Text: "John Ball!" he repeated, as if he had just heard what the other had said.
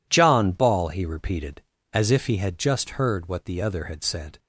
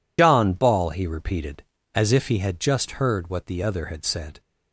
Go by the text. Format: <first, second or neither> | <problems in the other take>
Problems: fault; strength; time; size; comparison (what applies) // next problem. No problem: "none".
first | loses the start of "John"; at 0.1 s; 85 ms